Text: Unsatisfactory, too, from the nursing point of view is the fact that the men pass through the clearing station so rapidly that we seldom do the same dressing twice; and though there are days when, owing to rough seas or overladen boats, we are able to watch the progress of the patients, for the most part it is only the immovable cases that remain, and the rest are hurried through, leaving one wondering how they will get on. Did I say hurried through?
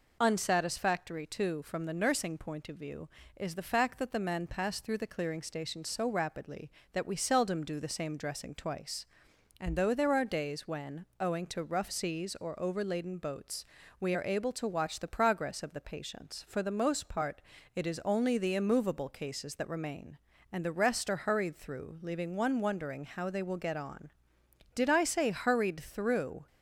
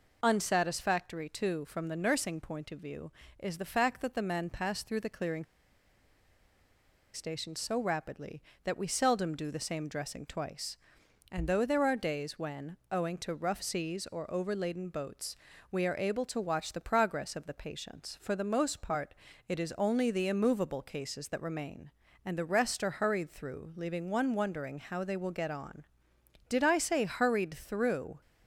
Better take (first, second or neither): first